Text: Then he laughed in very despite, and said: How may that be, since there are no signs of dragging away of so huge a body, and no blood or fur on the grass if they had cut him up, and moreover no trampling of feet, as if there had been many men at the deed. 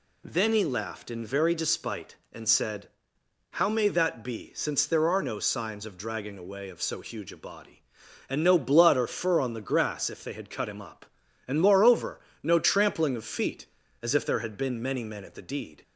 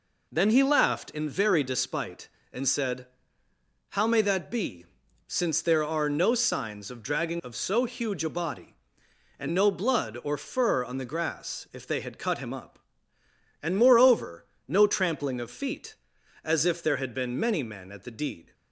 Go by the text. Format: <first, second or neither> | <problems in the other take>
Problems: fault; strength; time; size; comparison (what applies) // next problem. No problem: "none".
first | skips "away"; at 7.4 s // pauses between "moreover" and "no"; slight; at 14.4 s; 0.22 s long; slight in the first